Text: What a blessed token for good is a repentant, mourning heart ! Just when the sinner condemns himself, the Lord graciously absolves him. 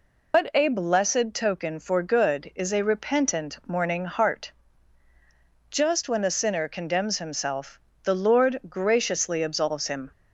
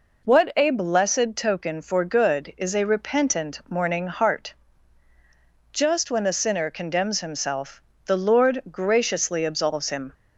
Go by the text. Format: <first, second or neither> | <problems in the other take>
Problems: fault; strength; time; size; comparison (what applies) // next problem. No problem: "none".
second | loses the start of "What"; at 0.3 s; 115 ms